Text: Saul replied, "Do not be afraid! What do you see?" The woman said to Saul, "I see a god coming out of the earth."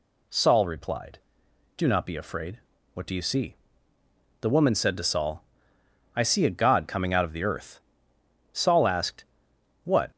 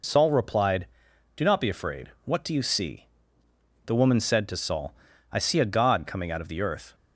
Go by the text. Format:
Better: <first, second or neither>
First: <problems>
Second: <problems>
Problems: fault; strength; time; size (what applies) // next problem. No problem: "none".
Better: second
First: goes on to say "Saul asked What"; from 8.5 s on; 1.5 s long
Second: none